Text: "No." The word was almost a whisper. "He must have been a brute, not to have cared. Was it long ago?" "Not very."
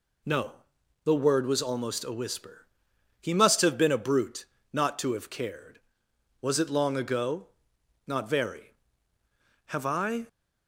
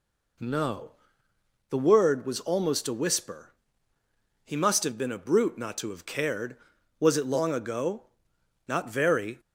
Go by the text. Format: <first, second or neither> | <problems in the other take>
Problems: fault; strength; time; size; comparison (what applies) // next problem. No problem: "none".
second | goes on to say "Have I"; noticeable; from 9.6 s on; 0.62 s long